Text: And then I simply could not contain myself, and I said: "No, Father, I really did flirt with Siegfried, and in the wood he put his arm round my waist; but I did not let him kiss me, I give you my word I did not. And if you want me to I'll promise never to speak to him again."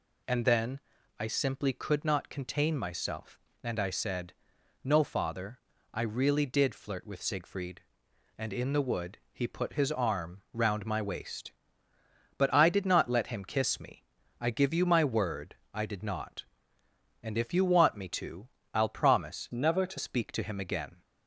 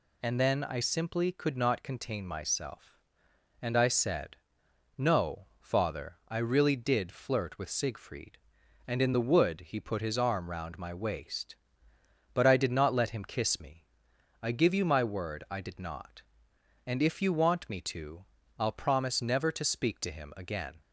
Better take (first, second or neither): second